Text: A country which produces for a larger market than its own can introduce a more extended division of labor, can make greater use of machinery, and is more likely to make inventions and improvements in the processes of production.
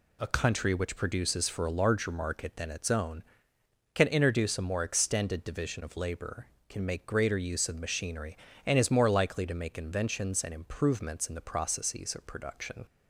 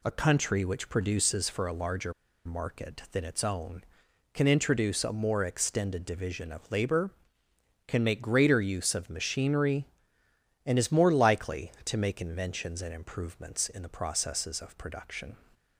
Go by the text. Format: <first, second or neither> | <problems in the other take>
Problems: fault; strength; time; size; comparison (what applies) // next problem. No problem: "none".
first | pauses between "larger" and "market"; slight; at 2.1 s; 0.33 s long